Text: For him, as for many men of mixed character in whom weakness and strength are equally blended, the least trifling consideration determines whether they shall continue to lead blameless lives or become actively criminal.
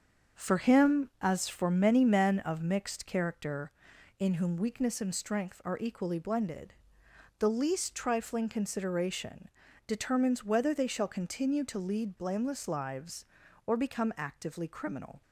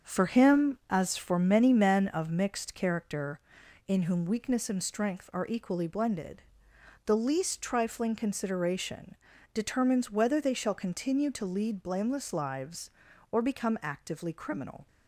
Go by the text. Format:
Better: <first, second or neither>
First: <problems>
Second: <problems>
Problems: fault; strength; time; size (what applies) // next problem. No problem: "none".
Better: neither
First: starts louder than the rest; until 1.4 s; 7 dB // pauses between "consideration" and "determines"; at 9.4 s; 0.38 s long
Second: starts louder than the rest; until 1.1 s; 7 dB // pauses between "consideration" and "determines"; at 9.1 s; 0.38 s long